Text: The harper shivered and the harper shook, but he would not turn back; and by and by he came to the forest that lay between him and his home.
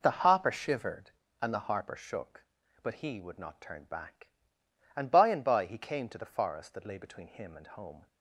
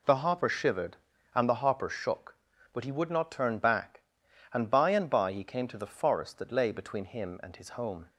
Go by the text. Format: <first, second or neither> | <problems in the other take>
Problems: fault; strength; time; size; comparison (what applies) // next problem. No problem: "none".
second | skips "his"; at 7.6 s